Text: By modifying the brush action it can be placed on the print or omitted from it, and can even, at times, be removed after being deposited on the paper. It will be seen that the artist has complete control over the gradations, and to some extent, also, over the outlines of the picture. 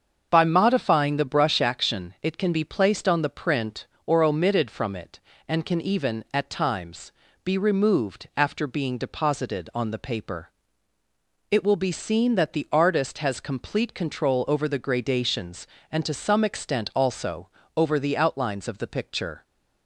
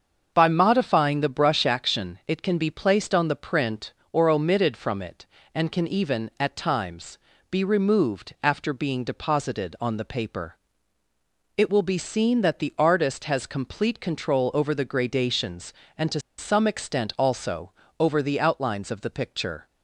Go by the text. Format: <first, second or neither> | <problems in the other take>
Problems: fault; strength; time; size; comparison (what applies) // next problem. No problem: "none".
first | starts louder than the rest; until 1.3 s; 6.5 dB; also in the first // pauses between "to" and "some"; slight; at 16.1 s; 0.19 s long